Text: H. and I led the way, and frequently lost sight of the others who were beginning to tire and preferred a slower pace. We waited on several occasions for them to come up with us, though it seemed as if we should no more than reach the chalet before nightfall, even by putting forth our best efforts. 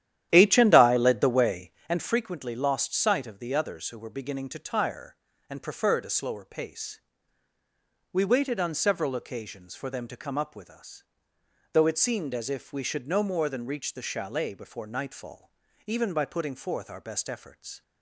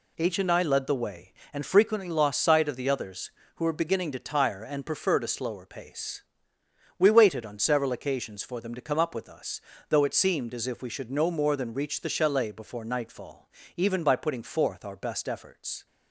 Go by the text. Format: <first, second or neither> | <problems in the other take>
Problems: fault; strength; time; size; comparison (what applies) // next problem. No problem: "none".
second | starts louder than the rest; strong; until 2.0 s; 11.5 dB